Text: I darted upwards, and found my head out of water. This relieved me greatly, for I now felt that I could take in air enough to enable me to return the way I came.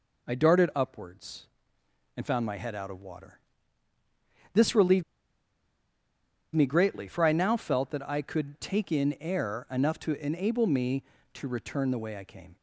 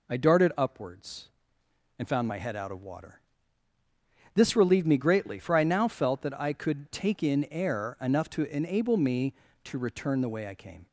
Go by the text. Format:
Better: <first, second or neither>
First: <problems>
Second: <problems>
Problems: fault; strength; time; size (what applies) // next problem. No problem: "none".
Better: second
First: pauses between "relieved" and "me"; strong; at 5.0 s; 1.5 s long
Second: none